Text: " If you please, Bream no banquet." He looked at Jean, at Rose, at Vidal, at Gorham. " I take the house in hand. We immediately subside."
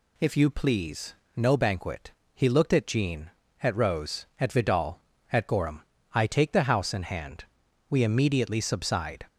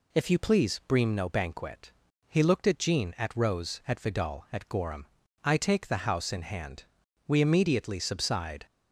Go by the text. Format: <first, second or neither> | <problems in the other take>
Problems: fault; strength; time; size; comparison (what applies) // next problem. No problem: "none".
second | skips "Bream"; at 1.2 s